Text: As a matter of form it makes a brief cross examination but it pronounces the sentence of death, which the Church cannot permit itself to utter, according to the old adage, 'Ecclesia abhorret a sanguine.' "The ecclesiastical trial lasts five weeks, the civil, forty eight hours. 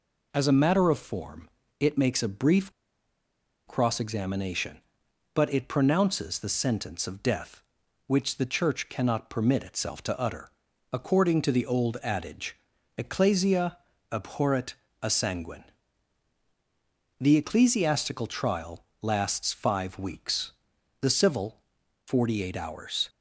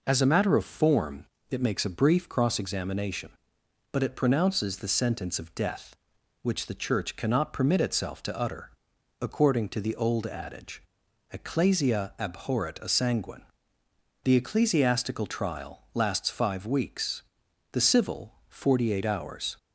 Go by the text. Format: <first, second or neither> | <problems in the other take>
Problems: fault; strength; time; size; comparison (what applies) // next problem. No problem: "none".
second | pauses between "form" and "it"; slight; at 1.4 s; 0.32 s long; slight in the second // pauses between "brief" and "cross"; noticeable; at 2.7 s; 0.95 s long // pauses between "Ecclesia" and "abhorret"; slight; at 13.7 s; 0.36 s long // pauses between "abhorret" and "a"; slight; at 14.7 s; 0.26 s long // pauses between "trial" and "lasts"; slight; at 18.8 s; 0.16 s long